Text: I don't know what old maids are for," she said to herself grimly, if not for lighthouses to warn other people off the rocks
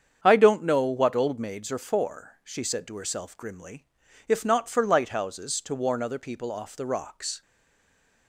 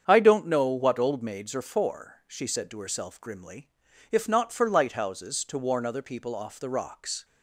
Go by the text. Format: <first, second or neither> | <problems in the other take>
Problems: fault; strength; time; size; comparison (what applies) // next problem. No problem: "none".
second | starts louder than the rest; strong; until 1.2 s; 8 dB; strong in the second // stays silent after the last word; slight; from 7.4 s on; 0.8 s long